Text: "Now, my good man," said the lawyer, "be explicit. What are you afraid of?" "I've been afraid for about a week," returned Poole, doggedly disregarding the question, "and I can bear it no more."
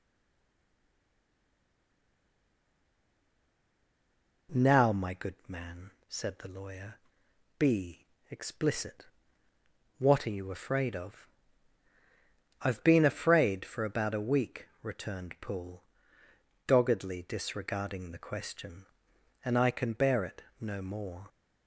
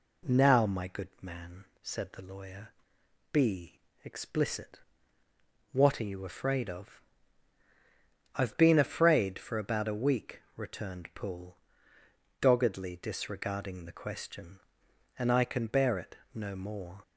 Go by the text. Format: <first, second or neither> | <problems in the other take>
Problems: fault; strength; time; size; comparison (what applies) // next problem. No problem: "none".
second | stays silent before the first word; strong; until 4.4 s; 4.4 s long // pauses between "be" and "explicit"; slight; at 8.0 s; 0.22 s long; slight in the second // pauses between "it" and "no"; slight; at 20.4 s; 0.16 s long; slight in the second